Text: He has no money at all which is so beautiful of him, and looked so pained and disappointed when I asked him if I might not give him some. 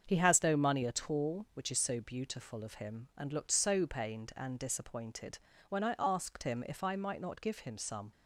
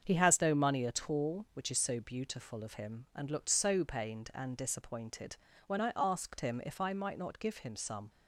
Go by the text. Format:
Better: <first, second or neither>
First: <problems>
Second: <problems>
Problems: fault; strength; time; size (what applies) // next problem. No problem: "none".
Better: neither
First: starts louder than the rest; until 1.0 s; 7 dB // pauses between "disappointed" and "when"; slight; at 5.3 s; 0.30 s long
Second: starts louder than the rest; until 1.0 s; 7 dB // pauses between "disappointed" and "when"; slight; at 5.3 s; 0.30 s long